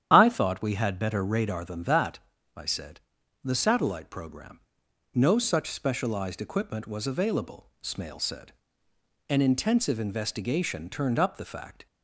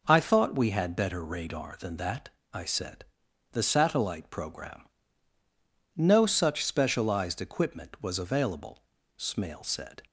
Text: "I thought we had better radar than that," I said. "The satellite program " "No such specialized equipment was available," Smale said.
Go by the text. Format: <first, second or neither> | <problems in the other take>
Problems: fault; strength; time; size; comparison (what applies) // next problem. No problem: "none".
second | starts louder than the rest; strong; until 1.1 s; 10 dB // goes on to say "An intensive investigation turned up the fact"; strong; from 9.3 s on; 2.5 s long